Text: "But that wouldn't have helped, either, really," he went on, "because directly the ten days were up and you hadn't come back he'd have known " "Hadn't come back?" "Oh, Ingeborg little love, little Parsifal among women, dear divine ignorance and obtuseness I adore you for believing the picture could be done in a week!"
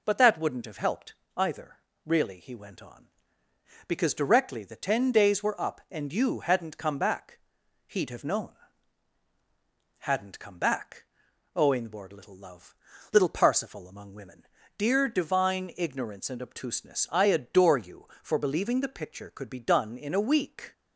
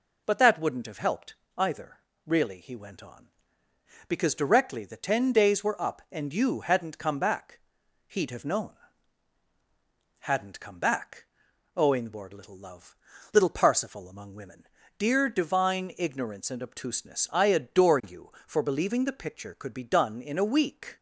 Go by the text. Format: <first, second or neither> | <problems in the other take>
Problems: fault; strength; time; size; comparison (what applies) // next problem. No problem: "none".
neither | pauses between "back" and "he'd"; noticeable; the same in both